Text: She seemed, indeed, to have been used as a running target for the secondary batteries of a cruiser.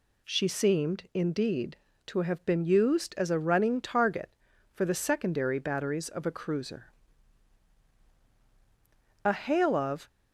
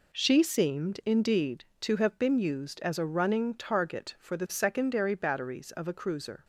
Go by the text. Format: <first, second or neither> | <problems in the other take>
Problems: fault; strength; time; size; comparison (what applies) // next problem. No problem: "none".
second | goes on to say "A hail of"; noticeable; from 9.2 s on; 0.84 s long